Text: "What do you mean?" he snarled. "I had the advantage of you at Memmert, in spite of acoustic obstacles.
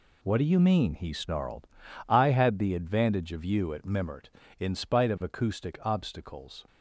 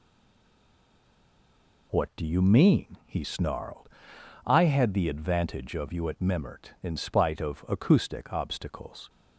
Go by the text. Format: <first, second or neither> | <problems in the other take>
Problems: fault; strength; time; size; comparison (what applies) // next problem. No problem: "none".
first | stays silent before the first word; noticeable; until 1.9 s; 1.9 s long